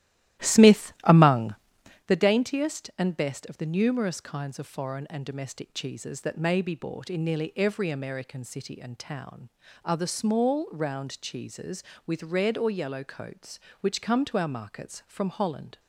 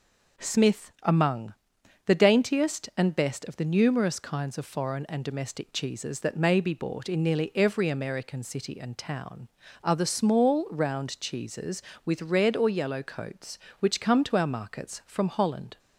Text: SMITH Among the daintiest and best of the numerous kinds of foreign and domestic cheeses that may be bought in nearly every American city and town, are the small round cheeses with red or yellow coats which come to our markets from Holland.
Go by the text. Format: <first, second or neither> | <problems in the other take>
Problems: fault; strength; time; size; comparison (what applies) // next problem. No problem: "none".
second | starts louder than the rest; strong; until 2.2 s; 14 dB // pauses between "Among" and "the"; noticeable; at 1.5 s; 0.50 s long; noticeable in the second